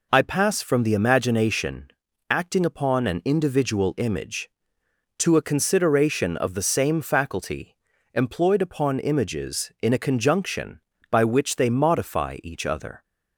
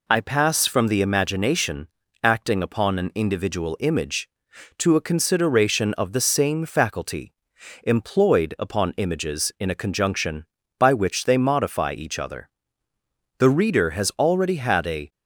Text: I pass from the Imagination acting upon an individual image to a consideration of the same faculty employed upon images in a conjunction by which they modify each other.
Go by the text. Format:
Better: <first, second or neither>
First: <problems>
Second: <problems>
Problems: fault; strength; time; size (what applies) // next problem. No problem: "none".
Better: first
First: pauses between "Imagination" and "acting"; at 1.9 s; 0.40 s long // pauses between "faculty" and "employed"; at 7.7 s; 0.38 s long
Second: pauses between "Imagination" and "acting"; slight; at 1.8 s; 0.34 s long // pauses between "faculty" and "employed"; noticeable; at 7.3 s; 0.50 s long // goes on to say "The Reader has already had a"; strong; from 13.3 s on; 1.7 s long